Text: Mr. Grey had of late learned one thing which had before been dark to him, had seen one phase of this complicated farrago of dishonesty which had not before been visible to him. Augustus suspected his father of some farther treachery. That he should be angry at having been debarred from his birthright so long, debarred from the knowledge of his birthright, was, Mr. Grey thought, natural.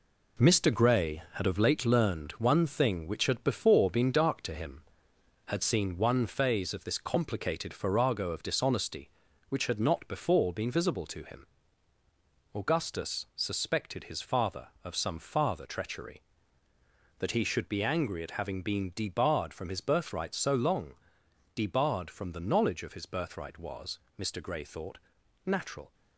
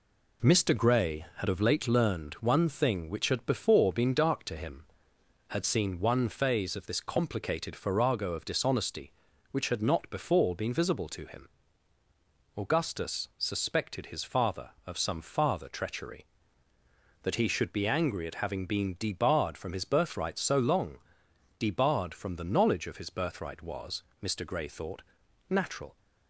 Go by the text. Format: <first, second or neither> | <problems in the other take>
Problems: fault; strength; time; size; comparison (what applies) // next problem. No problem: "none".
second | gets quieter; throughout; 6.5 dB